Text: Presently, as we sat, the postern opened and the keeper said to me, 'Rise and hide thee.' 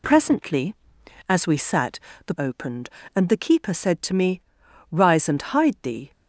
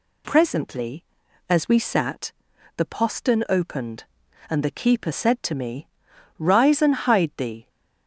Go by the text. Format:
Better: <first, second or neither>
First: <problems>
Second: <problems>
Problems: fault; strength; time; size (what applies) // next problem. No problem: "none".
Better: second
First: skips "postern"; at 2.3 s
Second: none